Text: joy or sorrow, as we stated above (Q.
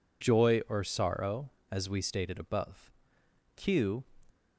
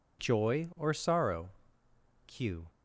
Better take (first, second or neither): first